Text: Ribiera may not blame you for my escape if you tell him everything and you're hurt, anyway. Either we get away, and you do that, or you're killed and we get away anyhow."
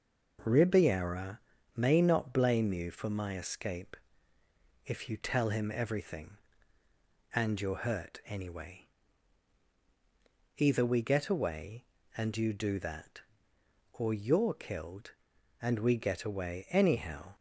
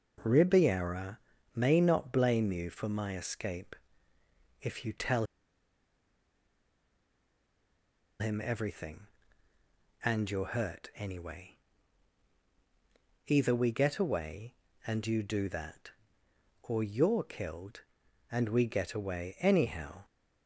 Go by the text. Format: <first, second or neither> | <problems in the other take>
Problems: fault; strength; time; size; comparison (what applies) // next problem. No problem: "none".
first | pauses between "Ribiera" and "may"; slight; at 1.1 s; 0.36 s long; slight in the first // pauses between "escape" and "if"; noticeable; at 3.7 s; 0.88 s long; noticeable in the first // pauses between "tell" and "him"; strong; at 5.2 s; 2.9 s long